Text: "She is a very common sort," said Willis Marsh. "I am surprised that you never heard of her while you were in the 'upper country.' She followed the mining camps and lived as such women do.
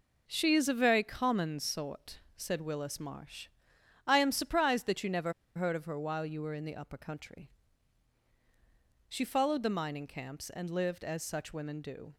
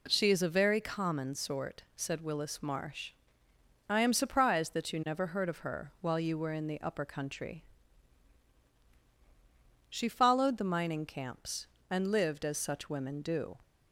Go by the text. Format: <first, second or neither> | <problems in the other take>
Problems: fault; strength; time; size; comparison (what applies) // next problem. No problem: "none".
second | pauses between "never" and "heard"; slight; at 5.3 s; 0.23 s long